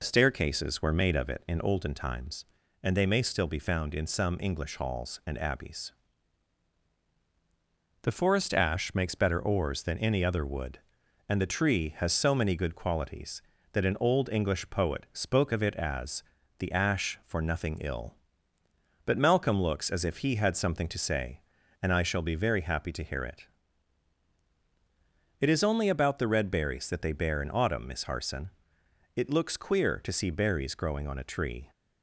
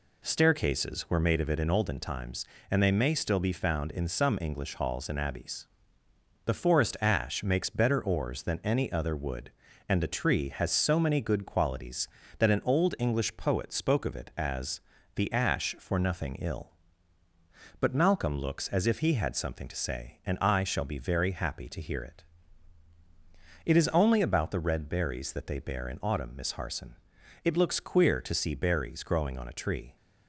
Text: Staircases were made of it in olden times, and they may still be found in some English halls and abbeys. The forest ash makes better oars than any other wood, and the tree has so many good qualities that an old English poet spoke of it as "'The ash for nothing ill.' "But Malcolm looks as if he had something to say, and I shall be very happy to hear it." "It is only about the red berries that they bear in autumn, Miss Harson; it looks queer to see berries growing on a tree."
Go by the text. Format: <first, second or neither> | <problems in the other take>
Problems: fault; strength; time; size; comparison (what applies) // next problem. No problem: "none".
neither | pauses between "as" and "The"; slight; the same in both